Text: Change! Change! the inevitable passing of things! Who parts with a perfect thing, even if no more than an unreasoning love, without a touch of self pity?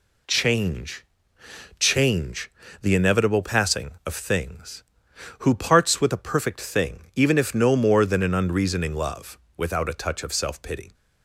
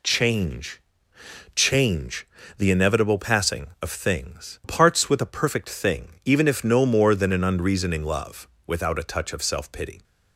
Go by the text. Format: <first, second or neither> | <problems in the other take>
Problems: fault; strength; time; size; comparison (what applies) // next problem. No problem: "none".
first | skips "Who"; at 4.6 s